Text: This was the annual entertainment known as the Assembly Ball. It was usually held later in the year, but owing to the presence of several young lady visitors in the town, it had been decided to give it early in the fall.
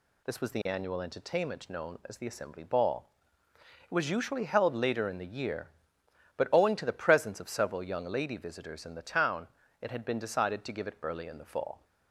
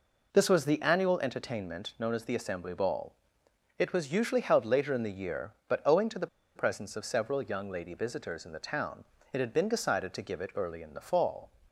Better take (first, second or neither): first